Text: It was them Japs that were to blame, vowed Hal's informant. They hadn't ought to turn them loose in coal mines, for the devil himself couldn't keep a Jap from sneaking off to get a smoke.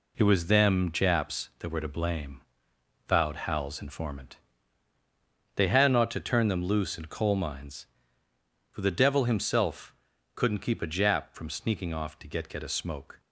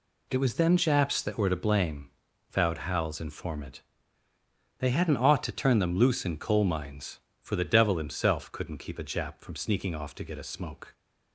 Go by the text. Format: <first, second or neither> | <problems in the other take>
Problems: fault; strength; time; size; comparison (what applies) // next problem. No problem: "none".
second | pauses between "himself" and "couldn't"; at 9.9 s; 0.40 s long // says "get" twice; at 12.4 s